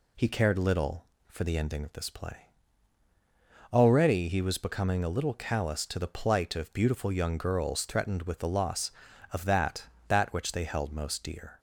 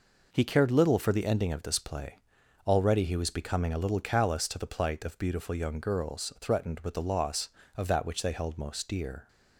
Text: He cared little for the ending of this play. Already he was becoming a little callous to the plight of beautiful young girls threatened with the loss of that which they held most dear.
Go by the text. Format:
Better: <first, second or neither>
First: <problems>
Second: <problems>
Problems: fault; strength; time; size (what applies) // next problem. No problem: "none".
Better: second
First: says "that" twice; at 10.0 s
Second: none